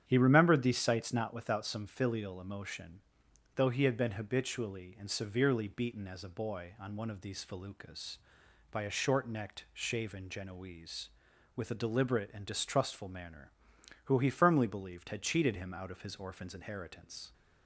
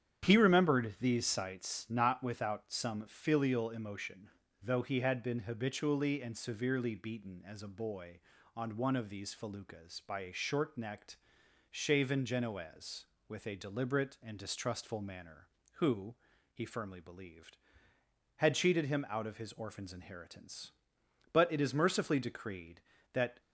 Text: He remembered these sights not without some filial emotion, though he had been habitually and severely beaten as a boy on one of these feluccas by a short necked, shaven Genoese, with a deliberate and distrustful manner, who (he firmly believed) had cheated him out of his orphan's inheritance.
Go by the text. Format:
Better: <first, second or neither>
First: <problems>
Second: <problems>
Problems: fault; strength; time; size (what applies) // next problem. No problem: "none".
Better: first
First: starts louder than the rest; strong; until 1.0 s; 9 dB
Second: starts louder than the rest; strong; until 1.3 s; 9.5 dB // goes on to say "But it is mercifully decreed that"; strong; from 21.3 s on; 2.0 s long